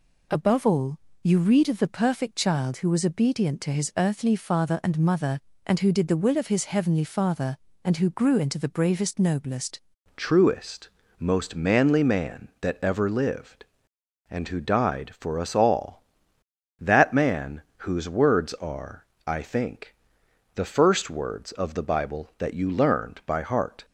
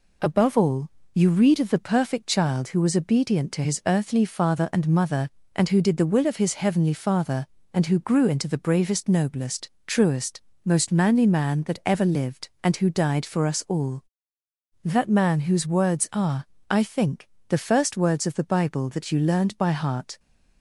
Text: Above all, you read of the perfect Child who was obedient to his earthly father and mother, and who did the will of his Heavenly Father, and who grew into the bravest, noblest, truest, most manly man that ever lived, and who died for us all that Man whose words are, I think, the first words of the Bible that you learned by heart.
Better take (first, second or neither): second